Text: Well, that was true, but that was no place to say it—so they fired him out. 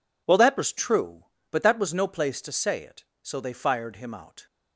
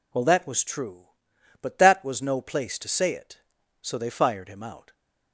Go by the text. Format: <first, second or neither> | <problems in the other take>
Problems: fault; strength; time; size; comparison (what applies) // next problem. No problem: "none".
neither | none